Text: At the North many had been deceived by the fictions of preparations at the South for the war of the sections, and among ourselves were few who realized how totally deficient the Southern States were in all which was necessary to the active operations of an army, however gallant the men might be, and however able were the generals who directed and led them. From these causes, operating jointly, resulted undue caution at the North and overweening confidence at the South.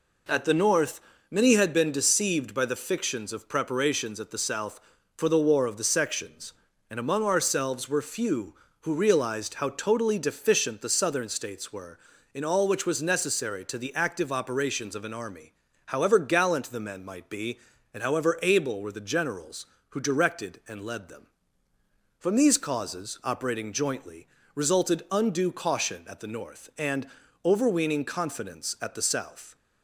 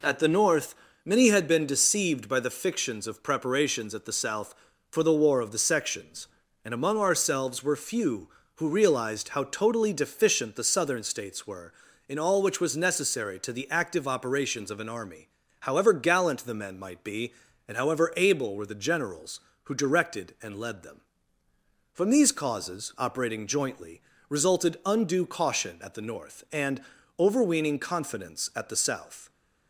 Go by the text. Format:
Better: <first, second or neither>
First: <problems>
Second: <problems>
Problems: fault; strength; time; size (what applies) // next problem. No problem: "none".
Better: neither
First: pauses between "North" and "many"; slight; at 0.9 s; 0.32 s long // pauses between "and" and "overweening"; at 27.0 s; 0.38 s long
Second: pauses between "North" and "many"; slight; at 0.7 s; 0.32 s long // pauses between "and" and "overweening"; at 26.8 s; 0.38 s long